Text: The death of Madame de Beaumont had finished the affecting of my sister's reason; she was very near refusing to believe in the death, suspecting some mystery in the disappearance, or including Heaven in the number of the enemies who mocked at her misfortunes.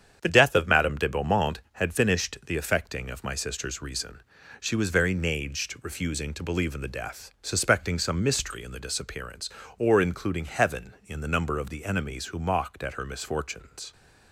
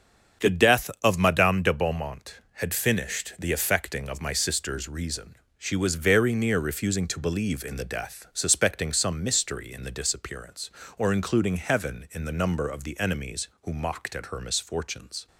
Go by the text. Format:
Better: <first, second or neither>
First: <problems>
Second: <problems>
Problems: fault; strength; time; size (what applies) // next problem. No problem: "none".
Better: second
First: starts louder than the rest; strong; until 1.2 s; 8.5 dB // says "naged" for "near"; at 5.1 s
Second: starts louder than the rest; strong; until 1.5 s; 7.5 dB